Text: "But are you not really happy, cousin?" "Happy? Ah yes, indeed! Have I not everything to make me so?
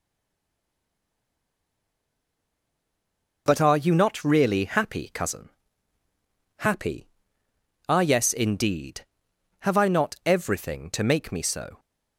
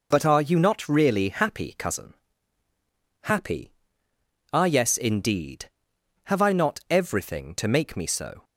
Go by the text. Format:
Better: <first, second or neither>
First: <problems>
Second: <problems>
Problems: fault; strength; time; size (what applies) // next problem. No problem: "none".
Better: second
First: stays silent before the first word; strong; until 3.4 s; 3.4 s long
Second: none